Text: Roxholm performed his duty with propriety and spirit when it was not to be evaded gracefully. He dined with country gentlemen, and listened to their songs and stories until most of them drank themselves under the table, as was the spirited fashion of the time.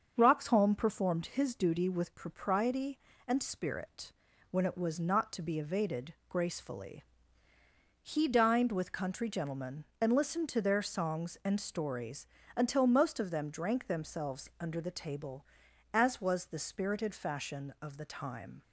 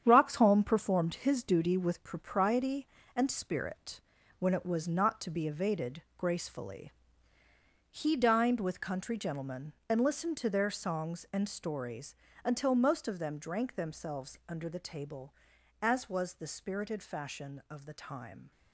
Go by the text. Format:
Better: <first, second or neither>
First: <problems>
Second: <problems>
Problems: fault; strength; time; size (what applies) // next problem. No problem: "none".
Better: first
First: starts louder than the rest; until 1.1 s; 6.5 dB // pauses between "spirit" and "when"; at 4.1 s; 0.38 s long // pauses between "evaded" and "gracefully"; slight; at 6.1 s; 0.16 s long // pauses between "stories" and "until"; slight; at 12.2 s; 0.30 s long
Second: gets quieter; strong; throughout; 8 dB // starts louder than the rest; strong; until 1.0 s; 8.5 dB // pauses between "spirit" and "when"; at 4.0 s; 0.38 s long // pauses between "evaded" and "gracefully"; slight; at 6.0 s; 0.16 s long // pauses between "stories" and "until"; slight; at 12.1 s; 0.30 s long